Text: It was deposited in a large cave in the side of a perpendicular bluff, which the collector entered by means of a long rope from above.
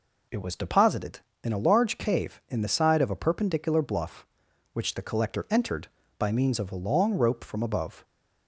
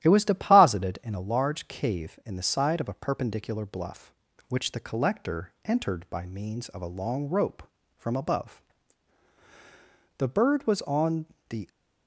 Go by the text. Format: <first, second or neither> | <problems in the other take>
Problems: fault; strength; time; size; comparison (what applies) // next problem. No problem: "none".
first | starts louder than the rest; strong; until 1.0 s; 12 dB // goes on to say "The bird was on the"; from 10.1 s on; 1.5 s long